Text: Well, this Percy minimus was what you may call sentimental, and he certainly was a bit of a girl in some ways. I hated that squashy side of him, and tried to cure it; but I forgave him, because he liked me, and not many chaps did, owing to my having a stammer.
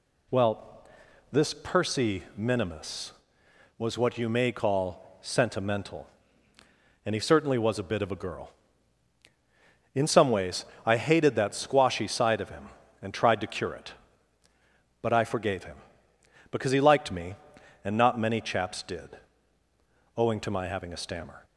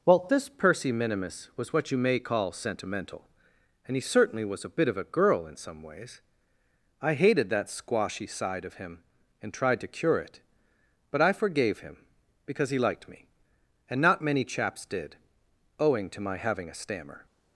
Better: first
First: none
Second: changes voice at "this"; from 0.2 s on; 17.0 s long

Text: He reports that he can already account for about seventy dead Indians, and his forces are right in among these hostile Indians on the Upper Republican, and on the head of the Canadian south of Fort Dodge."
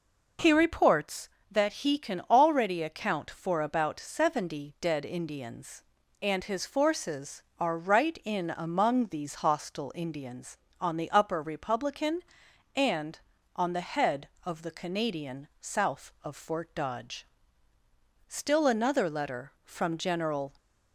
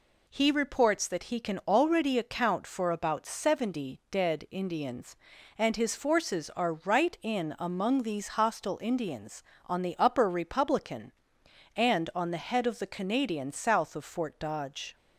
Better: second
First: goes on to say "Still another letter from General"; strong; from 18.2 s on; 2.2 s long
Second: none

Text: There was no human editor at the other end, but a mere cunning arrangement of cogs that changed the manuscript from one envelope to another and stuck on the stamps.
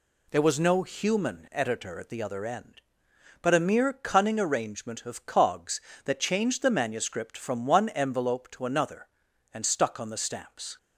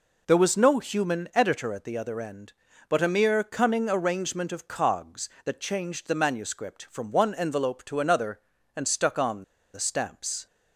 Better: first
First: none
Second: pauses between "on" and "the"; slight; at 9.4 s; 0.30 s long

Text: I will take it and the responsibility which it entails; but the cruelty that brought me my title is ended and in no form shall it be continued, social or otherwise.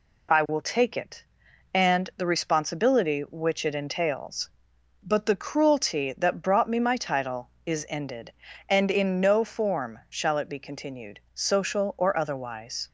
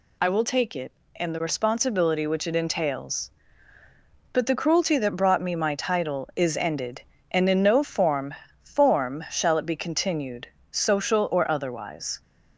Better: first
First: none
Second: says "form" twice; at 8.6 s

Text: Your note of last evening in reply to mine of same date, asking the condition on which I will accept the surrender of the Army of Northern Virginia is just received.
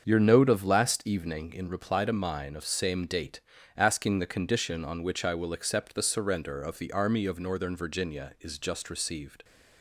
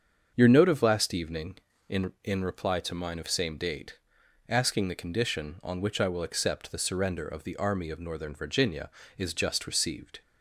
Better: first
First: starts louder than the rest; until 1.1 s; 7 dB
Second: starts louder than the rest; strong; until 1.3 s; 7 dB // says "in" twice; at 2.2 s

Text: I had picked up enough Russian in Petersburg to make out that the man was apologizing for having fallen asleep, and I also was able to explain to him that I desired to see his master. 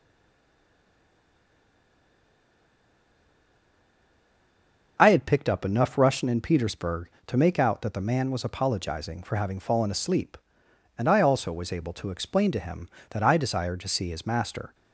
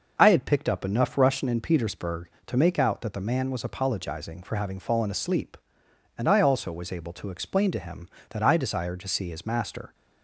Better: second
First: stays silent before the first word; strong; until 4.9 s; 4.9 s long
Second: none

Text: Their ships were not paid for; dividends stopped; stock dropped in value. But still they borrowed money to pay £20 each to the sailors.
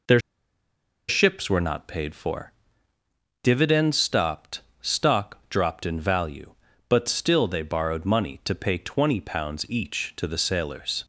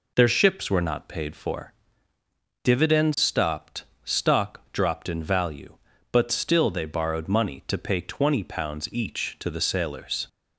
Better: second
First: pauses between "Their" and "ships"; noticeable; at 0.1 s; 0.89 s long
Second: none

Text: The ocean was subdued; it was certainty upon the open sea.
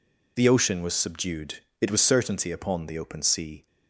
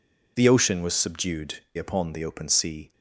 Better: first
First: none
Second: skips "it was certainty"; at 1.6 s

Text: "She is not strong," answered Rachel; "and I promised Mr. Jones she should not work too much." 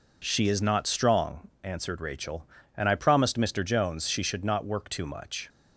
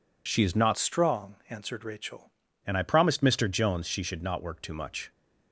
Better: first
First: none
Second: changes voice from "strong" to "Rachel"; from 0.7 to 2.3 s; 1.6 s long

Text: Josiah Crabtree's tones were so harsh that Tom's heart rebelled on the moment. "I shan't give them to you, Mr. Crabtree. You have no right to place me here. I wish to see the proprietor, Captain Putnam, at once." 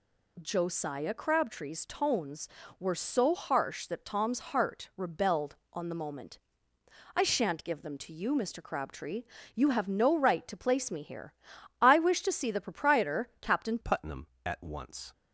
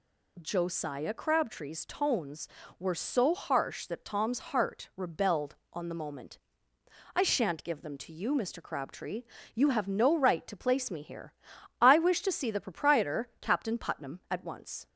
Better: second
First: changes voice at "Putnam"; from 13.8 s on; 1.3 s long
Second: none

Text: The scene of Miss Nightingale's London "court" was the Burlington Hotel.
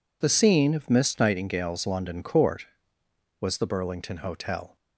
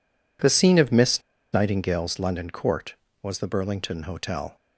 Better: first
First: none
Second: pauses between "Miss" and "Nightingale's"; slight; at 1.2 s; 0.31 s long

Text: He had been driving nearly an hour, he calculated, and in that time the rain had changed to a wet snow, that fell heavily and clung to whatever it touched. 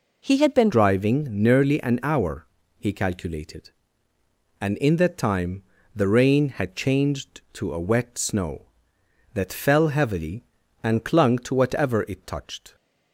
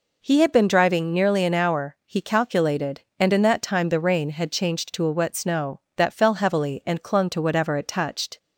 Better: second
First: changes voice at "driving"; from 0.7 s on; 12.0 s long // pauses between "time" and "the"; slight; at 5.6 s; 0.32 s long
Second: none

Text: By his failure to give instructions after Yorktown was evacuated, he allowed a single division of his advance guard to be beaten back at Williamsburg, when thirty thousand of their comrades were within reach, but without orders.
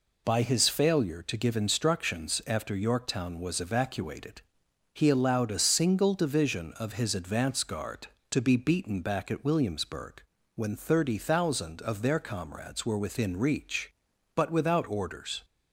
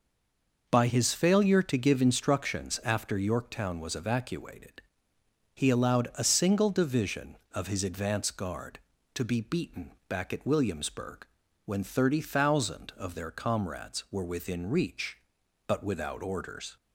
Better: first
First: none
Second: stays silent before the first word; slight; until 0.6 s; 0.6 s long // pauses between "beaten" and "back"; slight; at 9.9 s; 0.18 s long

